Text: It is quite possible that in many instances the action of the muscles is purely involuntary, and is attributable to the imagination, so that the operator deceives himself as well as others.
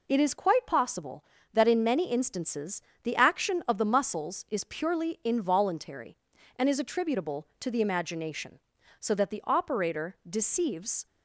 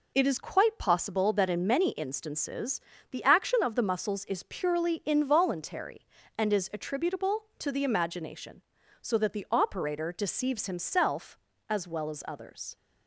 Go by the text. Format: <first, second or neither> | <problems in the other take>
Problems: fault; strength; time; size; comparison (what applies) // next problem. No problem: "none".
second | pauses between "instances" and "the"; slight; at 2.8 s; 0.22 s long; slight in the second // stops before "himself as well as others"; at 11.0 s